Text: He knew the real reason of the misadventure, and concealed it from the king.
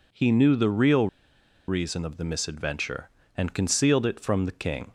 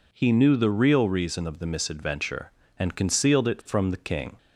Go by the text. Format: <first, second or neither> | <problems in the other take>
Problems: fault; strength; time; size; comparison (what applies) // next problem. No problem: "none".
second | pauses between "real" and "reason"; noticeable; at 1.0 s; 0.60 s long